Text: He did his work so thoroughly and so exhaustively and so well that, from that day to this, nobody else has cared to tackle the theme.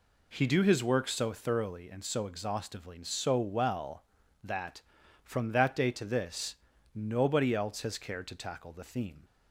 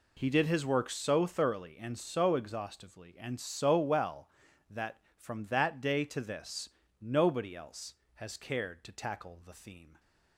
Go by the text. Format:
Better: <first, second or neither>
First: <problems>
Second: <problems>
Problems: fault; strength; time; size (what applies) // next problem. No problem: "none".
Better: second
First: says "do" for "did"; at 0.4 s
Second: none